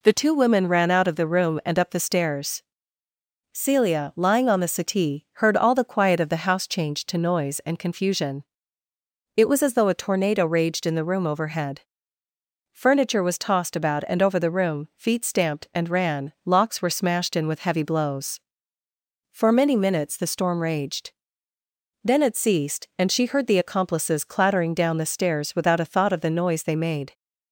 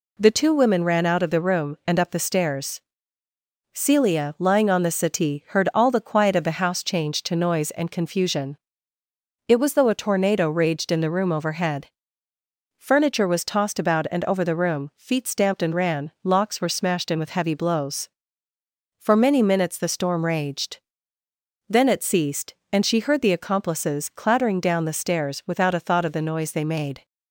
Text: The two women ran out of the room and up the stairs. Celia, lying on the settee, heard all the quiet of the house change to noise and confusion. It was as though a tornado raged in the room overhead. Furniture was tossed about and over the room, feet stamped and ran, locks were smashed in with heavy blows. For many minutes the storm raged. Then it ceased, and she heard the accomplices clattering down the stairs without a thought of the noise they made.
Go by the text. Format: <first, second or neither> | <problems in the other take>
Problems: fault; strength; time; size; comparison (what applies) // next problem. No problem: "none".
first | skips "as"; at 9.7 s